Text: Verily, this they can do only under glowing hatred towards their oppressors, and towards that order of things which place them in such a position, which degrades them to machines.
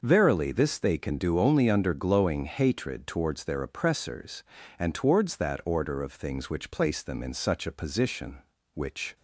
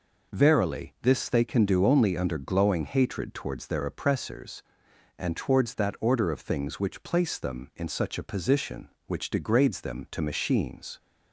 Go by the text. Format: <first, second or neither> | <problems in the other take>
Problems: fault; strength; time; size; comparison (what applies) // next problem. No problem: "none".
second | stops before "degrades them to machines"; at 9.1 s